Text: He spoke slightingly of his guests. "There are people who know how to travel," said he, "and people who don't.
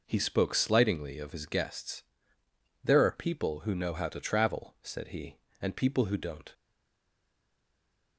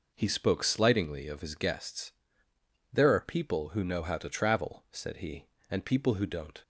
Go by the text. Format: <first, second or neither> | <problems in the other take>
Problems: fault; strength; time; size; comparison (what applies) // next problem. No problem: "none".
second | stays silent after the last word; noticeable; from 6.5 s on; 1.6 s long